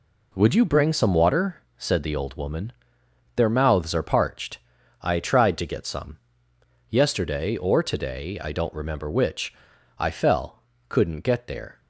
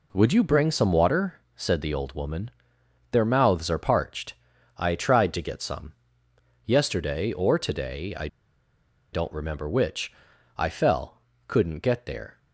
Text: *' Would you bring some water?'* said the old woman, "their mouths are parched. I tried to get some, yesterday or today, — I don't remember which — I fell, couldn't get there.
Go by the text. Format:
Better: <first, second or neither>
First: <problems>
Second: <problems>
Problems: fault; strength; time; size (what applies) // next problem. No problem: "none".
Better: first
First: none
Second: pauses between "I" and "don't"; noticeable; at 8.2 s; 0.85 s long